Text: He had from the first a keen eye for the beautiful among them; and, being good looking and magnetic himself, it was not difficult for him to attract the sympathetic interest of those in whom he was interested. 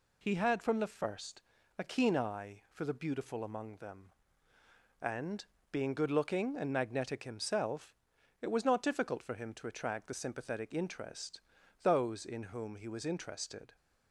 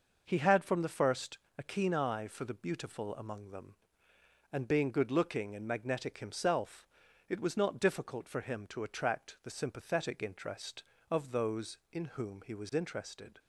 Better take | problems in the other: second | pauses between "first" and "a"; at 1.4 s; 0.38 s long; slight in the second // skips "of"; at 11.6 s

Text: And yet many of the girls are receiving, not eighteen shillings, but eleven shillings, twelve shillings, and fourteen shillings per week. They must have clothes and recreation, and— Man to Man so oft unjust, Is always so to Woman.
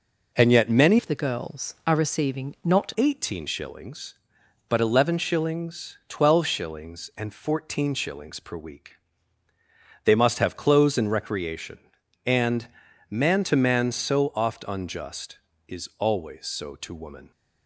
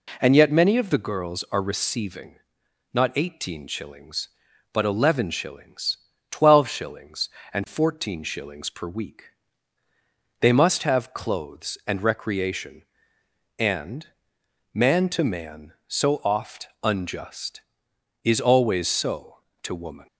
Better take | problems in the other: second | changes voice from "of" to "not"; from 0.9 to 2.9 s; 2.0 s long

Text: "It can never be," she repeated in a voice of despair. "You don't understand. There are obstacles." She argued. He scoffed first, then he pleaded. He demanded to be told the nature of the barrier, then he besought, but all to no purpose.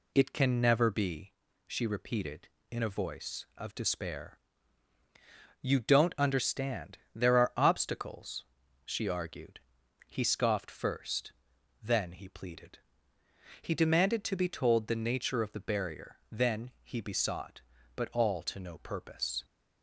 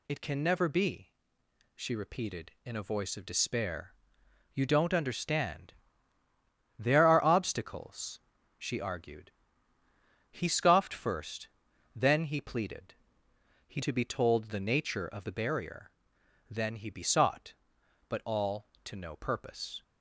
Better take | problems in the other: first | skips "demanded"; at 13.8 s

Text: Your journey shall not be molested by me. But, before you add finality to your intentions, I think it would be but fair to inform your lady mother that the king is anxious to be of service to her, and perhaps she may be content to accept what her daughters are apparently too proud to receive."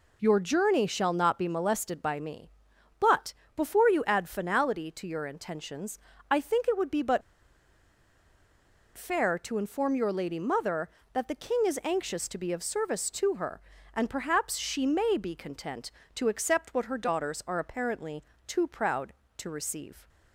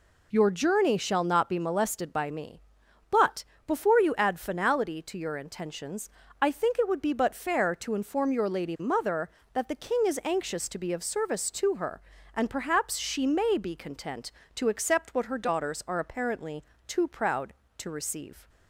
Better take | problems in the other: second | pauses between "but" and "fair"; strong; at 7.2 s; 1.7 s long // pauses between "apparently" and "too"; slight; at 18.2 s; 0.24 s long; slight in the second

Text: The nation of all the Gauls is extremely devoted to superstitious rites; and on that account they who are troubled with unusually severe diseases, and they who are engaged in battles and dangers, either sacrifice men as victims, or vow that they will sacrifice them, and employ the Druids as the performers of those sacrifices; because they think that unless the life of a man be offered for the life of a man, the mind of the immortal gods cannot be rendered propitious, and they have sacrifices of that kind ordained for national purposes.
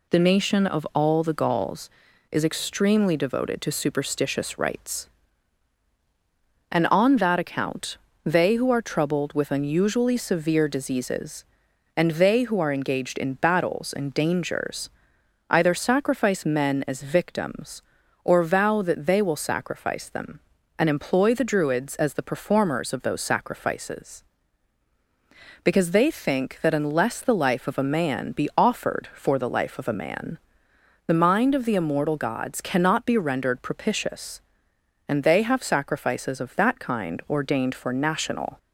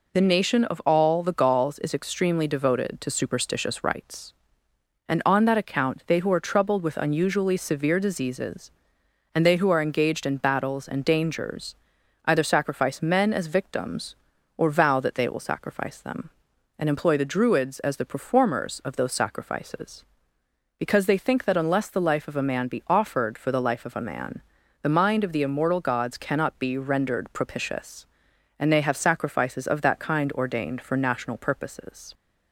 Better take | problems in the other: second | pauses between "account" and "they"; slight; at 7.9 s; 0.26 s long // stops before "purposes"; at 38.5 s

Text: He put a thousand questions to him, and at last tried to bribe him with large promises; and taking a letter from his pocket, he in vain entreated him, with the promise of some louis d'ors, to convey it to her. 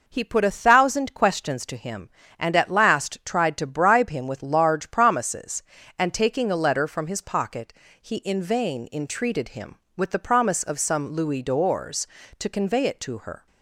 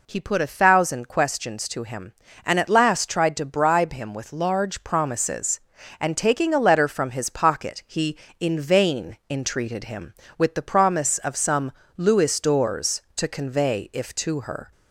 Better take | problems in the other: first | pauses between "some" and "louis"; slight; at 11.7 s; 0.26 s long // says "if" for "it"; at 13.9 s

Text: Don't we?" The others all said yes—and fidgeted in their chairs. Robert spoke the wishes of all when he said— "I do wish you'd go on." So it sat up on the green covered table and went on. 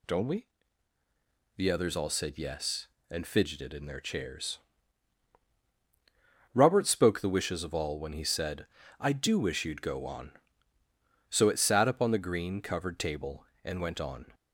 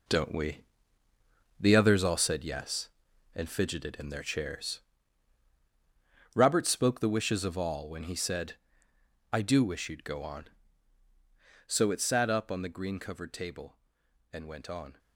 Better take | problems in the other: first | gets quieter; strong; throughout; 9.5 dB

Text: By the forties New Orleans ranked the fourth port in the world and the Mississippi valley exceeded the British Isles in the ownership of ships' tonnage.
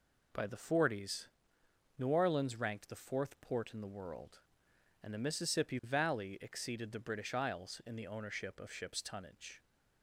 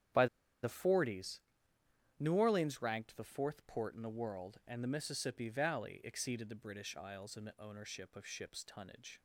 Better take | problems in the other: first | starts louder than the rest; strong; until 2.2 s; 9.5 dB // pauses between "By" and "the"; slight; at 0.2 s; 0.36 s long // pauses between "forties" and "New"; noticeable; at 1.4 s; 0.76 s long; noticeable in the first

